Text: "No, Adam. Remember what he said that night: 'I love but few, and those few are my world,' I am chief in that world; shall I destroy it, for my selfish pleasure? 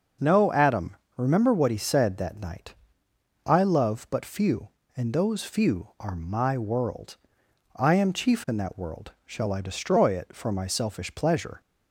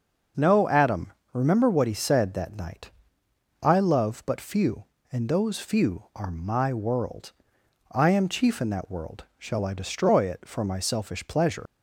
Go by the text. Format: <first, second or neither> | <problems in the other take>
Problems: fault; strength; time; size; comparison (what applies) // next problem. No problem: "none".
first | starts louder than the rest; noticeable; until 1.5 s; 6 dB; noticeable in the first // leaves "pleasure" unfinished; at 11.6 s; 75 ms